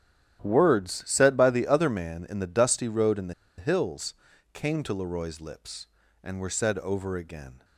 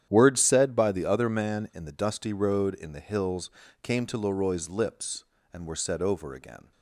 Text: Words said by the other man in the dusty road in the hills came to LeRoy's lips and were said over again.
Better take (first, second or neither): second